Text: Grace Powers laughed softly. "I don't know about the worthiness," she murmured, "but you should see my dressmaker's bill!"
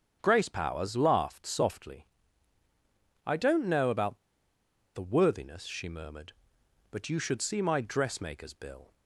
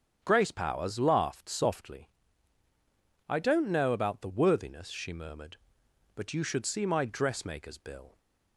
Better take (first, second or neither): second